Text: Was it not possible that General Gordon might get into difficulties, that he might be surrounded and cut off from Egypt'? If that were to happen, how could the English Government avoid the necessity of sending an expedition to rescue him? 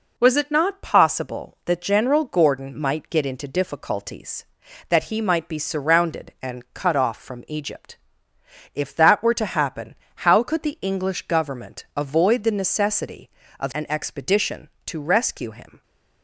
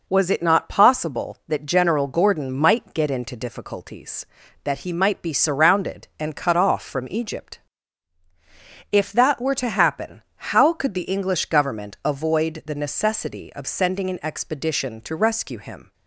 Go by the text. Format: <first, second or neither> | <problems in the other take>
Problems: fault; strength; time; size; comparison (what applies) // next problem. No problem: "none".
second | skips "sending"; at 13.7 s